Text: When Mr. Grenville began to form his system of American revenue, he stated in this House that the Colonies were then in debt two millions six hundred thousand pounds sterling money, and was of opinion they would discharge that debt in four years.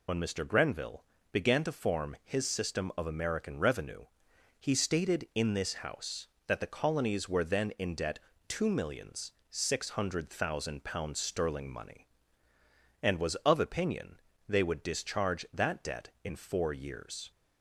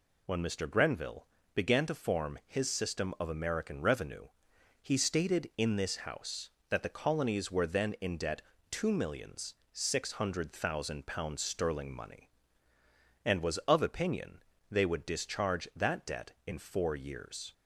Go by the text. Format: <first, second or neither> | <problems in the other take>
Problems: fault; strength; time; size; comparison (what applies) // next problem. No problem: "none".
second | loses the start of "When"; at 0.0 s; 60 ms // pauses between "Grenville" and "began"; slight; at 1.0 s; 0.26 s long; slight in the second // pauses between "debt" and "two"; slight; at 8.1 s; 0.30 s long; slight in the second // pauses between "millions" and "six"; slight; at 9.3 s; 0.18 s long; slight in the second // pauses between "opinion" and "they"; slight; at 14.2 s; 0.28 s long; slight in the second